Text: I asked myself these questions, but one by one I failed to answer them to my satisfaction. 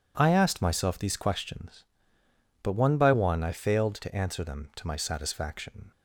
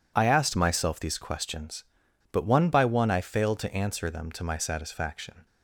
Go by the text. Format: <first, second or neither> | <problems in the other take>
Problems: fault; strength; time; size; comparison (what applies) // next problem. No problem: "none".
neither | none